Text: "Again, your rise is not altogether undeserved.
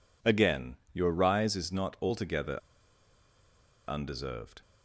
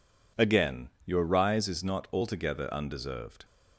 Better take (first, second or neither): second